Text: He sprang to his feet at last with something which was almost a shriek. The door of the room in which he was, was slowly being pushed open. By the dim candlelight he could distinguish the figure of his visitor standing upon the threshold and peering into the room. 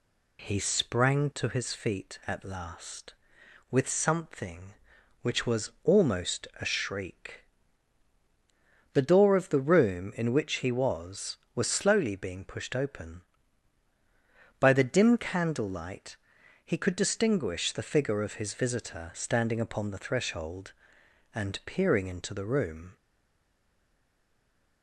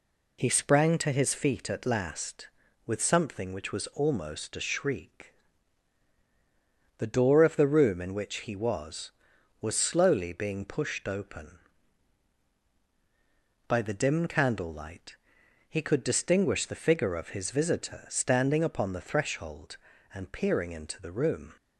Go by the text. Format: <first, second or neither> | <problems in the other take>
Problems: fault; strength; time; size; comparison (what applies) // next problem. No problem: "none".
second | pauses between "candlelight" and "he"; noticeable; at 16.1 s; 0.46 s long; noticeable in the second // stays silent after the last word; noticeable; from 22.9 s on; 1.9 s long